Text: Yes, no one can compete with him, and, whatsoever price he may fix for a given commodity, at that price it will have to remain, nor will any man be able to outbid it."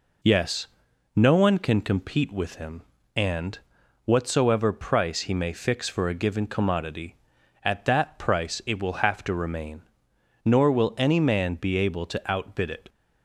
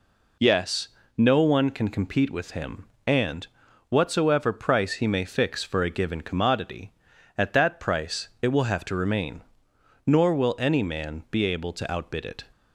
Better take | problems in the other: neither | none

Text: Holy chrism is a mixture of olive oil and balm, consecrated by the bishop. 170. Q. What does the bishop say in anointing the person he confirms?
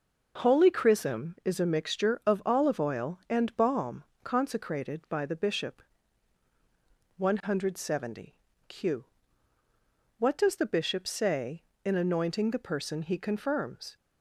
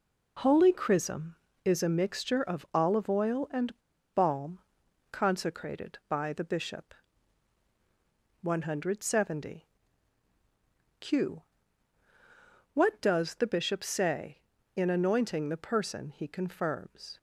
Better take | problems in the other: first | pauses between "and" and "balm"; at 3.7 s; 0.42 s long

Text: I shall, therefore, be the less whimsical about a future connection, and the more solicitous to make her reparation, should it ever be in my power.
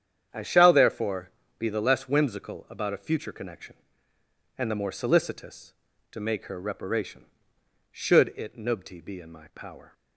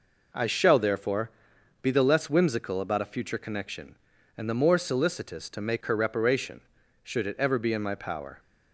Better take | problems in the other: second | starts louder than the rest; strong; until 1.6 s; 8.5 dB // says "nubti" for "ever"; at 8.5 s

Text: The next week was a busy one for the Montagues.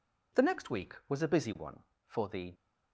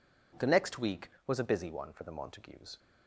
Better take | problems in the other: second | stops before "Montagues"; at 2.5 s

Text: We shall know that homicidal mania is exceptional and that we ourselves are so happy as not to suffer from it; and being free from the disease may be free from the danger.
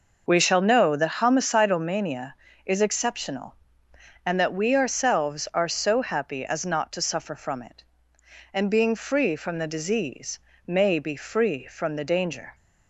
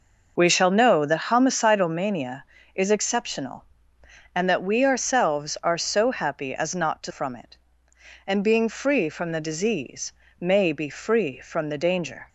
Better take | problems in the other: first | skips "suffer"; at 7.1 s // pauses between "disease" and "may"; slight; at 10.1 s; 0.28 s long; slight in the first

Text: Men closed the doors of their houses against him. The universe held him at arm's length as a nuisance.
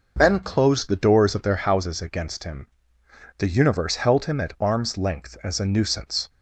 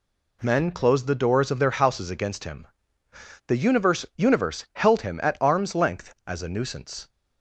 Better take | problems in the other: first | says "universe" twice; at 4.1 s

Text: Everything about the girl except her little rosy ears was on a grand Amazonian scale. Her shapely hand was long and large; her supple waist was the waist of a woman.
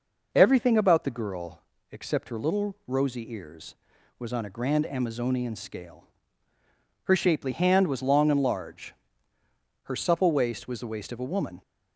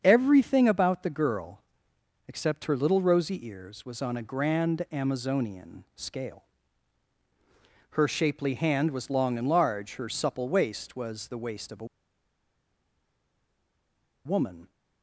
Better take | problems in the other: first | starts louder than the rest; strong; until 1.0 s; 7 dB // pauses between "girl" and "except"; noticeable; at 1.5 s; 0.68 s long; slight in the first // pauses between "a" and "woman"; strong; at 11.8 s; 2.3 s long

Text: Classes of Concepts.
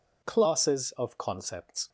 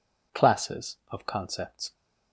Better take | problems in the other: neither | none

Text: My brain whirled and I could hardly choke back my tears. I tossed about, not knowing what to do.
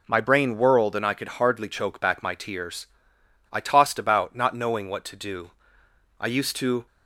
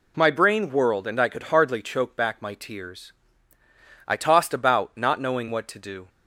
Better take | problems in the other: second | goes on to say "I used to"; noticeable; from 6.1 s on; 0.66 s long

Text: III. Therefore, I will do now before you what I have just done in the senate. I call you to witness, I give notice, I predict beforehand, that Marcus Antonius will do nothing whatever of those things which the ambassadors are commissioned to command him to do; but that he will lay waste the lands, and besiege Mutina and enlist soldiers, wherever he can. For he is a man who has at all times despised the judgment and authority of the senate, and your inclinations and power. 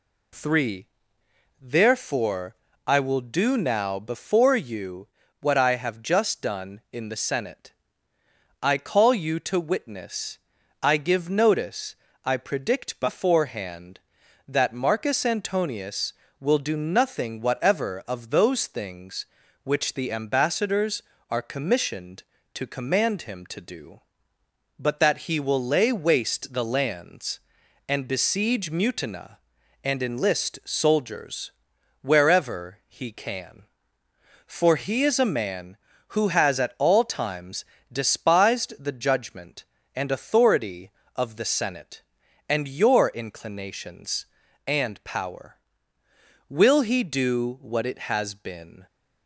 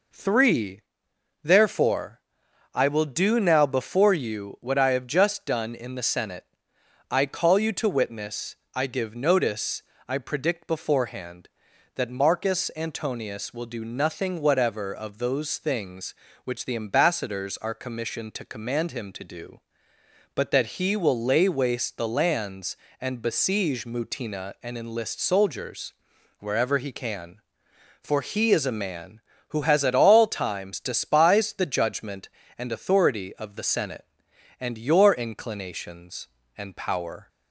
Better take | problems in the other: second | pauses between "you" and "what"; slight; at 5.0 s; 0.34 s long // pauses between "times" and "despised"; slight; at 37.6 s; 0.26 s long // goes on to say "Will he do what it has been"; strong; from 46.4 s on; 2.3 s long

